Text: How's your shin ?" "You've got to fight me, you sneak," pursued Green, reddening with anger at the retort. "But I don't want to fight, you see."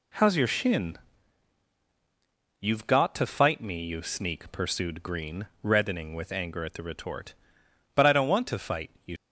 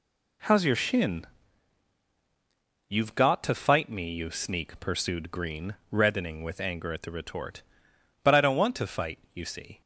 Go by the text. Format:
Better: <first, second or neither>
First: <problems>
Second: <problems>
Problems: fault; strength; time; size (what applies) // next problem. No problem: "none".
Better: second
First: stops before "see"; at 9.1 s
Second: none